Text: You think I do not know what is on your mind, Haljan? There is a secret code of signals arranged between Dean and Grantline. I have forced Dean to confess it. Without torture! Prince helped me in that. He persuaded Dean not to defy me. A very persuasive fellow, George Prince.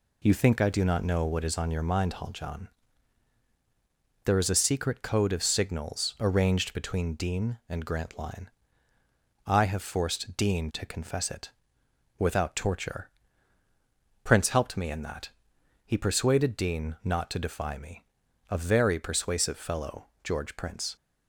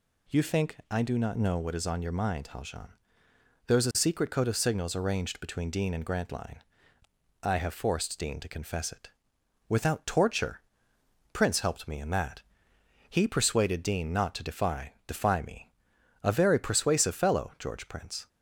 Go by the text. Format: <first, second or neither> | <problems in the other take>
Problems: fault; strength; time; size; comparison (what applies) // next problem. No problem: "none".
first | says "defy" twice; at 15.0 s